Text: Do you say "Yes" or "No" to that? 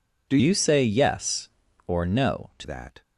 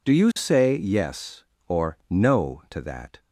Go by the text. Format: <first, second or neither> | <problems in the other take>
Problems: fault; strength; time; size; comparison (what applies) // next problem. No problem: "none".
second | changes voice from "you" to "to"; from 0.4 to 2.6 s; 2.2 s long